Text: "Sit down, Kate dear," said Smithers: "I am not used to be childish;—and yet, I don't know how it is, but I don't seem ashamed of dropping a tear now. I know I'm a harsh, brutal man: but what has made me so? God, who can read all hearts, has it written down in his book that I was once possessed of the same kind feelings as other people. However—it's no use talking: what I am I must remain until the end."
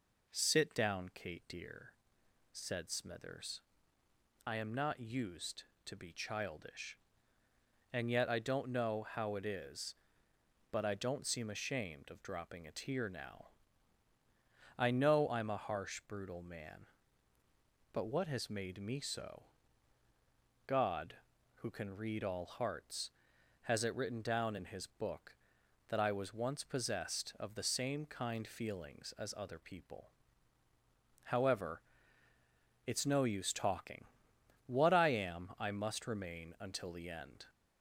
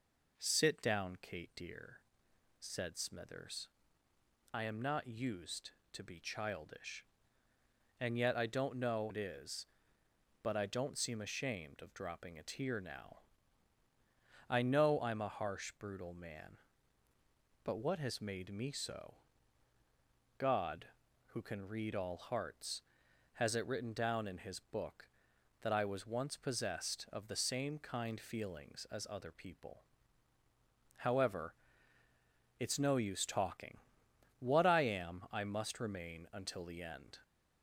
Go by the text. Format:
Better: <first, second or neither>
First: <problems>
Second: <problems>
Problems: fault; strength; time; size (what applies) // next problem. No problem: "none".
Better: first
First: none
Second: skips "how"; at 9.1 s